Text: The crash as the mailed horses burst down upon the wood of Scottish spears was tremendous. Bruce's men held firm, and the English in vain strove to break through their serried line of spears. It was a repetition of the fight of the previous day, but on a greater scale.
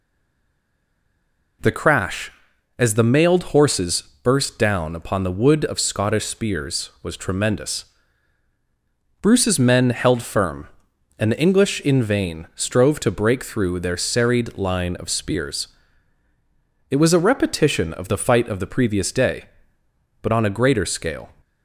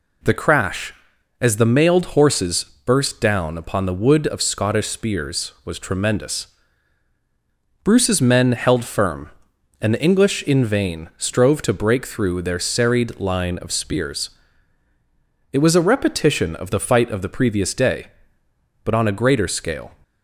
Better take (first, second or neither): second